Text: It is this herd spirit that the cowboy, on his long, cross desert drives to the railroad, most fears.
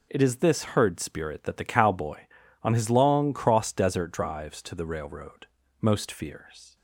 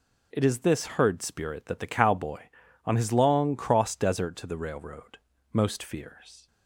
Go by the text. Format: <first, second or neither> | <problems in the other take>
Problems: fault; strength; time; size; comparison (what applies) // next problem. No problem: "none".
first | skips "drives"; at 4.3 s